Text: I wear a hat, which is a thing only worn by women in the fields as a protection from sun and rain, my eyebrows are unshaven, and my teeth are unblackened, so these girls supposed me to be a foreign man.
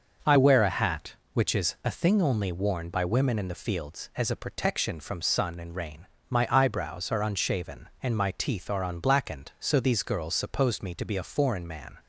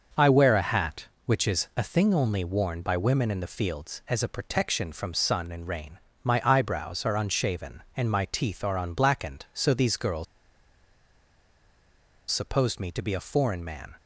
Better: first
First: starts louder than the rest; noticeable; until 1.3 s; 6 dB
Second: starts louder than the rest; until 1.2 s; 6 dB // pauses between "girls" and "supposed"; strong; at 10.2 s; 2.0 s long

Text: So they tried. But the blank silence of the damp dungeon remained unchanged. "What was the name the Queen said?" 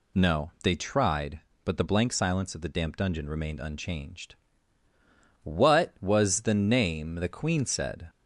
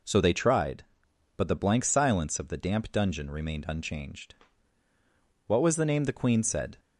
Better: second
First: says "No" for "So"; at 0.1 s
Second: none

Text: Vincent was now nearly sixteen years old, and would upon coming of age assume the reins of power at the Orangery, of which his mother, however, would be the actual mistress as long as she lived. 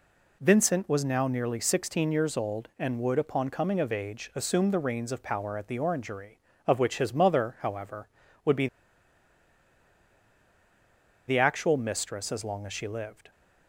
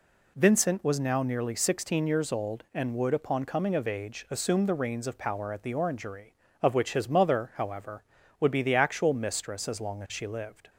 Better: second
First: pauses between "be" and "the"; strong; at 8.6 s; 2.6 s long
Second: none

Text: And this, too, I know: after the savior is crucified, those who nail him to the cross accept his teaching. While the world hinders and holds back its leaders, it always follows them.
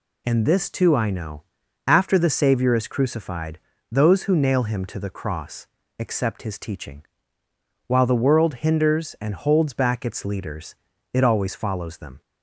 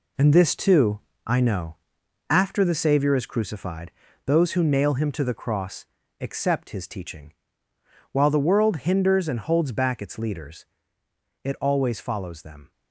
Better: first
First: pauses between "cross" and "accept"; slight; at 5.6 s; 0.32 s long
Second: gets quieter; strong; throughout; 8.5 dB // pauses between "cross" and "accept"; slight; at 5.8 s; 0.36 s long

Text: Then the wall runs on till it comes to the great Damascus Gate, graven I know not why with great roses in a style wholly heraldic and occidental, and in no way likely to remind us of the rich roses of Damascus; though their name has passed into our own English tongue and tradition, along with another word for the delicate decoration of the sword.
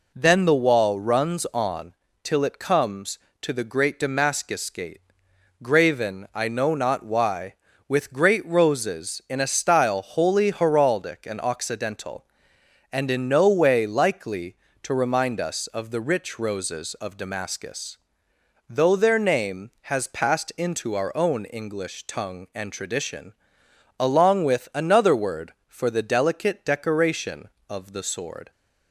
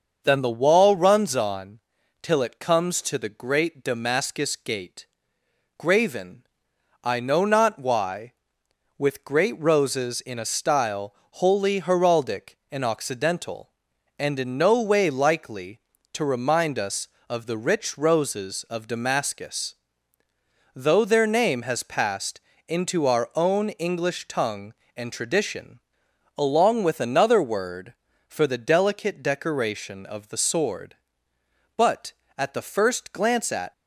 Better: first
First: pauses between "on" and "till"; slight; at 1.9 s; 0.30 s long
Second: starts louder than the rest; until 1.2 s; 6.5 dB // pauses between "on" and "till"; at 1.7 s; 0.42 s long // pauses between "graven" and "I"; noticeable; at 6.4 s; 0.58 s long // pauses between "style" and "wholly"; slight; at 11.1 s; 0.20 s long // pauses between "passed" and "into"; slight; at 22.4 s; 0.26 s long // goes on to say "But at the first glance at"; strong; from 31.7 s on; 1.9 s long

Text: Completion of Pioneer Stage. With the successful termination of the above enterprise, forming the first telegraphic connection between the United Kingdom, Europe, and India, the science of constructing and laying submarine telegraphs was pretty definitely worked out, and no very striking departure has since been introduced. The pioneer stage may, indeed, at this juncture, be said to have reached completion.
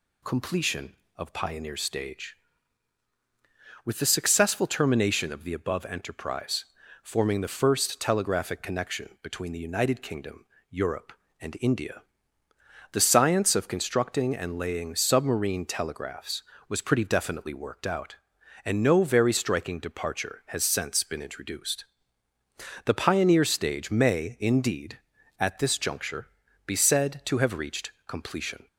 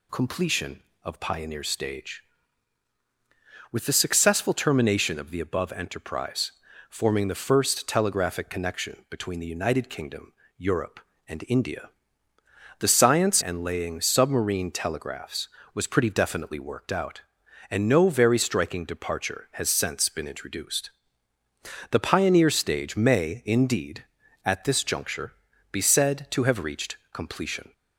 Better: first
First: pauses between "reached" and "completion"; slight; at 27.9 s; 0.16 s long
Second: skips "of constructing"; at 13.4 s // pauses between "reached" and "completion"; slight; at 26.9 s; 0.16 s long

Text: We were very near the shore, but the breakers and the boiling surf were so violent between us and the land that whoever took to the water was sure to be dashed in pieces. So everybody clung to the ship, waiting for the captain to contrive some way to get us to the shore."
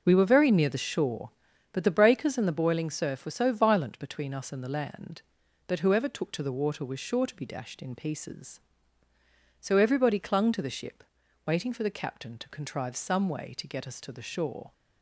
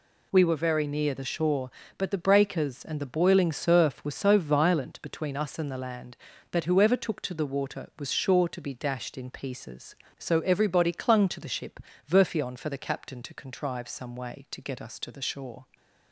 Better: first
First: none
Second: says "verfion" for "waiting"; at 12.0 s

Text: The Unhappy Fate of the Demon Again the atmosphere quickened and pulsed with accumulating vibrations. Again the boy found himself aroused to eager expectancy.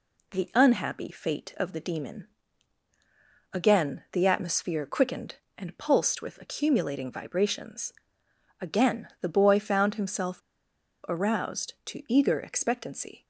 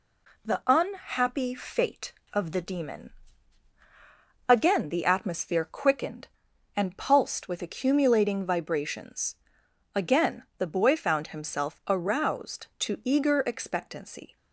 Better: second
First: pauses between "Demon" and "Again"; strong; at 2.2 s; 1.2 s long // pauses between "himself" and "aroused"; noticeable; at 10.4 s; 0.68 s long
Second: pauses between "Demon" and "Again"; strong; at 3.1 s; 1.3 s long

